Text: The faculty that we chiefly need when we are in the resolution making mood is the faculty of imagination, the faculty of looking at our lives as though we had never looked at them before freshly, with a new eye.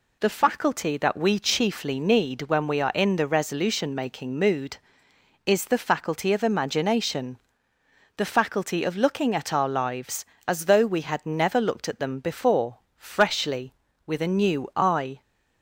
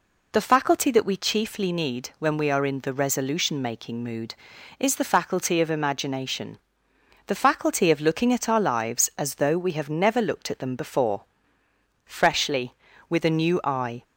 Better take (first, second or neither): first